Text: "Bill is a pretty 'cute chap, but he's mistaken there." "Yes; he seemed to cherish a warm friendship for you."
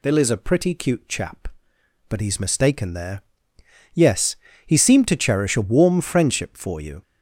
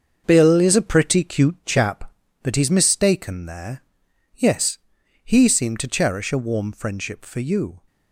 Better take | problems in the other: first | gets quieter; strong; throughout; 9 dB

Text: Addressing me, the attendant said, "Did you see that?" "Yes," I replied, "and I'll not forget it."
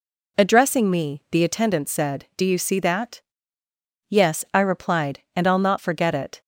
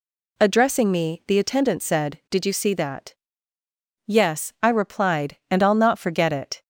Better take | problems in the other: second | says "Do" for "Did"; at 2.3 s

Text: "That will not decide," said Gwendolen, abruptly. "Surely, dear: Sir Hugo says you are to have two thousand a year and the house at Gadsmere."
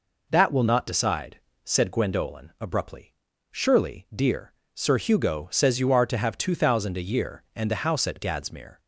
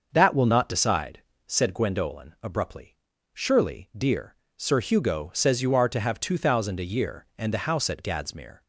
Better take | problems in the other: first | starts louder than the rest; until 1.1 s; 6.5 dB

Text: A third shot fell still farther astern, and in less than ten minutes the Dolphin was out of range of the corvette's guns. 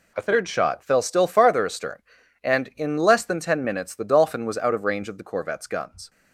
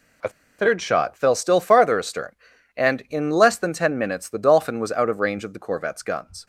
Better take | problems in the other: first | pauses between "A" and "third"; slight; at 0.2 s; 0.29 s long

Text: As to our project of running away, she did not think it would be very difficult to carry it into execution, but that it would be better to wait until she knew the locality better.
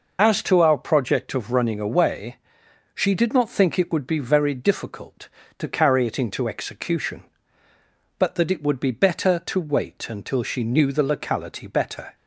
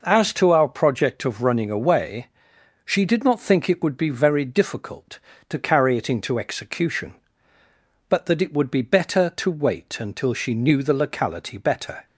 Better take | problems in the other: second | loses the start of "As"; at 0.1 s; 75 ms

